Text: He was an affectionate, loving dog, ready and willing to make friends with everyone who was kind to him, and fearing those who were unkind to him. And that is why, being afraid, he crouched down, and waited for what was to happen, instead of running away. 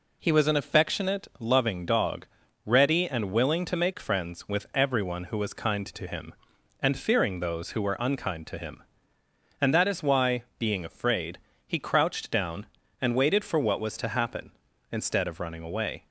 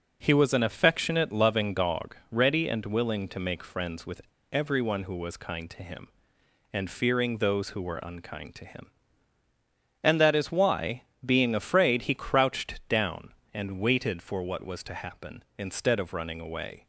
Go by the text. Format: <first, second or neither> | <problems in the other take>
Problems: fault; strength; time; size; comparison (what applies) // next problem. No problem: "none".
first | pauses between "with" and "everyone"; slight; at 4.2 s; 0.29 s long